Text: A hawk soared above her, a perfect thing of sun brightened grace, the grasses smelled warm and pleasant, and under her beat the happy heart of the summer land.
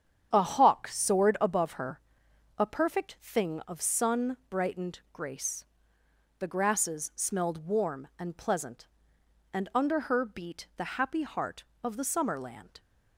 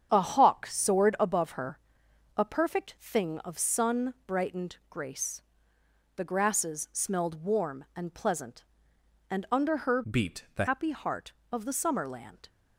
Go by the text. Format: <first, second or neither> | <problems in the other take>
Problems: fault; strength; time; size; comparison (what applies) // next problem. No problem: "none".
first | starts louder than the rest; strong; until 1.1 s; 8 dB; strong in the first // changes voice from "beat" to "the"; from 10.0 to 10.6 s; 0.6 s long